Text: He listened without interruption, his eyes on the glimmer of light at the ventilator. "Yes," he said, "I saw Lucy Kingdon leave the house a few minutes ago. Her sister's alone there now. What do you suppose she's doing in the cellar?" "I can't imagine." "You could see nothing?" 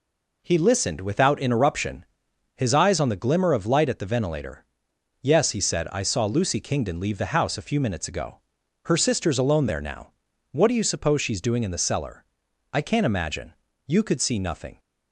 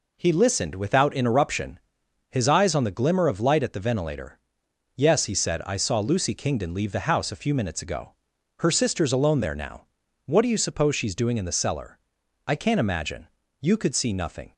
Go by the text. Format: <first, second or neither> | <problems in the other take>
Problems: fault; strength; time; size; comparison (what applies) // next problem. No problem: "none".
neither | none